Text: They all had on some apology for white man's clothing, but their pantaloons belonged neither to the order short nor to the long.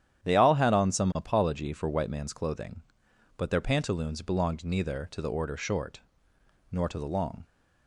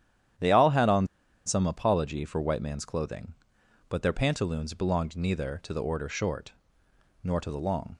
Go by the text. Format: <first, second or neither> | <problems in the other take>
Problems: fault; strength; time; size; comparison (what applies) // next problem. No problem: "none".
first | starts louder than the rest; strong; until 1.7 s; 10 dB; strong in the first // pauses between "on" and "some"; at 1.0 s; 0.39 s long // pauses between "short" and "nor"; noticeable; at 6.5 s; 0.72 s long; noticeable in the first